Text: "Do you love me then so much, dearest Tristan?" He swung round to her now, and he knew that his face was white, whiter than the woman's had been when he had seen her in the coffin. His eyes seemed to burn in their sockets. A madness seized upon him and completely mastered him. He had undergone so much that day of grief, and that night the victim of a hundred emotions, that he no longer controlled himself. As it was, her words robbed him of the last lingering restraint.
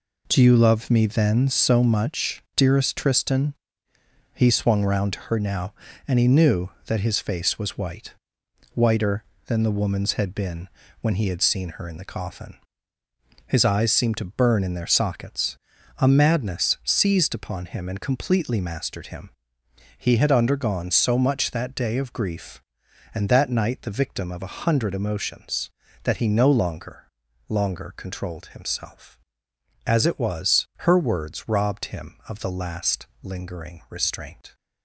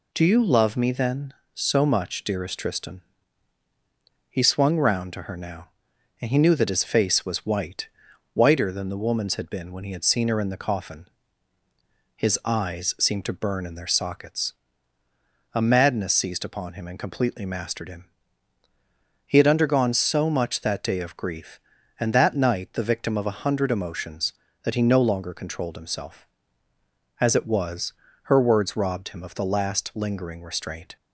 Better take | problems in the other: second | pauses between "been" and "when"; slight; at 10.6 s; 0.32 s long // says "longer" twice; at 27.4 s // pauses between "last" and "lingering"; slight; at 33.0 s; 0.16 s long

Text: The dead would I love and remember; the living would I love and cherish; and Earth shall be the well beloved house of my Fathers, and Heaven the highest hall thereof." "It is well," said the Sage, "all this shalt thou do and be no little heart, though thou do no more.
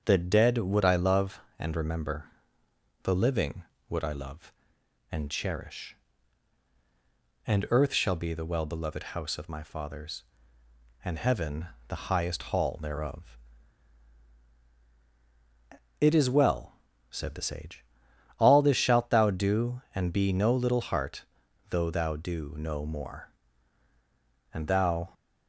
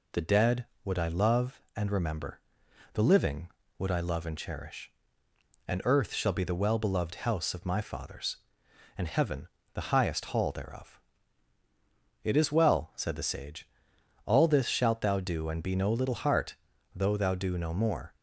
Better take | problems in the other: second | starts louder than the rest; until 1.0 s; 6.5 dB // pauses between "Heaven" and "the"; slight; at 11.6 s; 0.20 s long; slight in the second // goes on to say "And thou"; from 24.5 s on; 0.60 s long

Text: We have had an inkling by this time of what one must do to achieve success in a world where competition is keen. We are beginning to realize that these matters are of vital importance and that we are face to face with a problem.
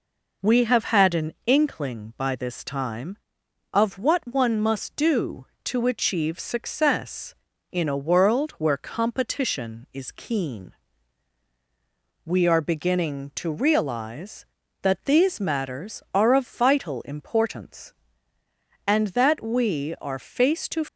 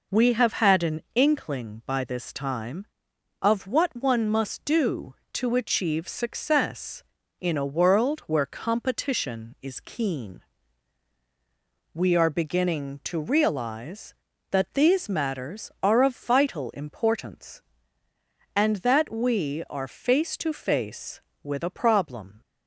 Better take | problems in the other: second | stops before "face with a problem"; at 20.8 s

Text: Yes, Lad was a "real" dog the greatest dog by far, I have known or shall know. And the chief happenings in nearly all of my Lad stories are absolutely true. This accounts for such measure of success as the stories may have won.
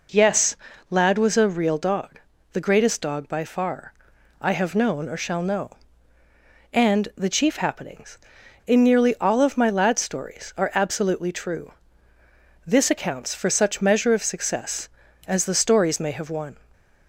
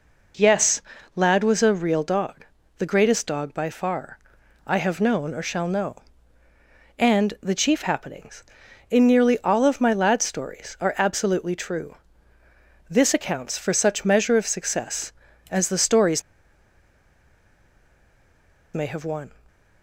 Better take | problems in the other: first | pauses between "dog" and "the"; slight; at 2.4 s; 0.34 s long; slight in the first // pauses between "stories" and "may"; strong; at 16.2 s; 2.5 s long

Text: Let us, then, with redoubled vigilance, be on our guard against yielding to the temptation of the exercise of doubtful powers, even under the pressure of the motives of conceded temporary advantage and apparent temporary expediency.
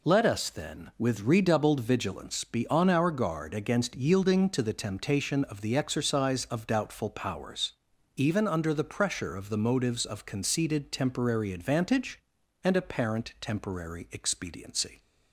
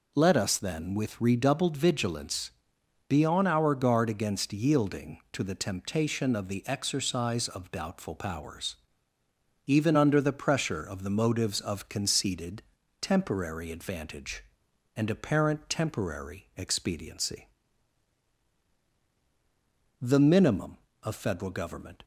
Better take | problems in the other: first | pauses between "conceded" and "temporary"; at 12.6 s; 0.38 s long // goes on to say "The minimum of Federal government"; strong; from 19.9 s on; 2.0 s long

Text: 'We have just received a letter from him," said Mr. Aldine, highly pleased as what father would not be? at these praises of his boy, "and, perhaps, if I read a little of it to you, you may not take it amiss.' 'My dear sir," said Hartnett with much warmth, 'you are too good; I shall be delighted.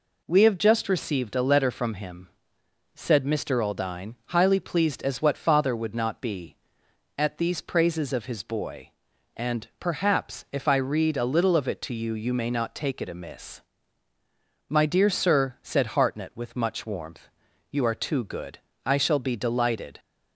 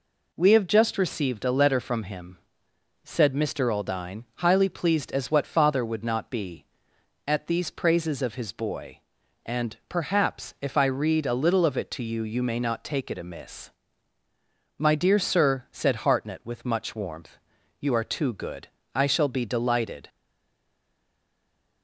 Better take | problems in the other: first | stays silent after the last word; noticeable; from 20.0 s on; 1.8 s long

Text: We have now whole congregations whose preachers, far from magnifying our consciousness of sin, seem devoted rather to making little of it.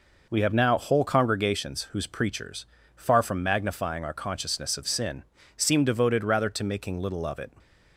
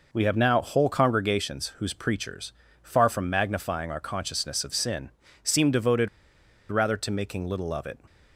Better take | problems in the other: first | pauses between "devoted" and "rather"; noticeable; at 6.0 s; 0.63 s long

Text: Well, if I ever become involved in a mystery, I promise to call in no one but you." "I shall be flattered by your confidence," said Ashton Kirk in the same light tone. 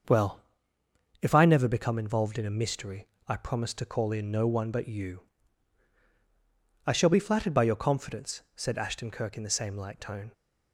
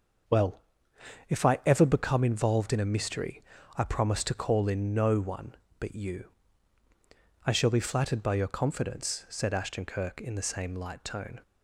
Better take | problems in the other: second | starts louder than the rest; until 1.8 s; 6.5 dB; also in the second // says "never" for "ever"; at 1.4 s

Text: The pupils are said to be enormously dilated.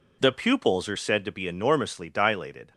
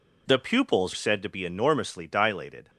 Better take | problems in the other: first | skips "are"; at 0.9 s

